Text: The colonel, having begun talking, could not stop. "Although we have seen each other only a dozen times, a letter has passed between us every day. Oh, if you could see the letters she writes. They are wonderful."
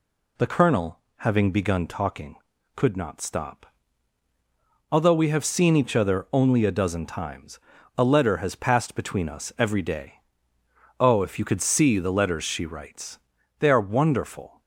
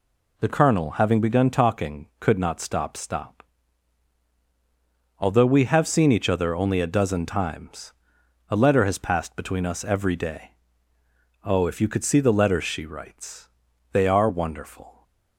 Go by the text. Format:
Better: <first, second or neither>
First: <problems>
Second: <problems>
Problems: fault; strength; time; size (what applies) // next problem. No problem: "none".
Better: first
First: none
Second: says "stop" twice; at 2.9 s